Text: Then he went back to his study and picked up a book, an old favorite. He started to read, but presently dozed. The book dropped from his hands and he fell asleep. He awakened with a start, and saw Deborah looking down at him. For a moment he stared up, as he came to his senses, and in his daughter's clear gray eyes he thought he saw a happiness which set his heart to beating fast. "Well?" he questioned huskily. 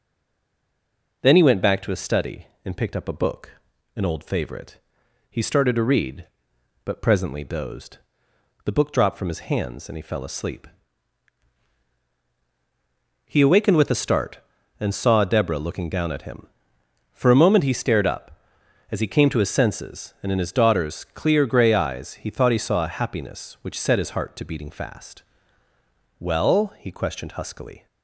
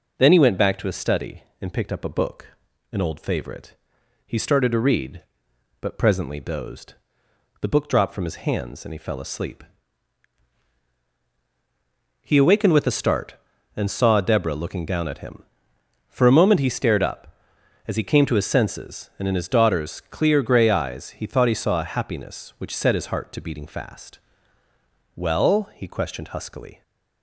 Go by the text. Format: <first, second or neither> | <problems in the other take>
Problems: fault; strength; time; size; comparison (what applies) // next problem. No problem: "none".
second | stays silent before the first word; noticeable; until 1.2 s; 1.2 s long